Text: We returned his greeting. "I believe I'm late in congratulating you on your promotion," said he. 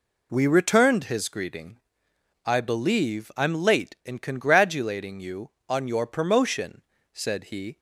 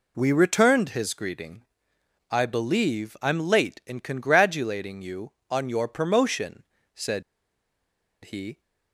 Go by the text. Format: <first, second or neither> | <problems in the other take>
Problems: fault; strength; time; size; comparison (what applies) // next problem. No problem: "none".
first | pauses between "said" and "he"; at 7.2 s; 1.0 s long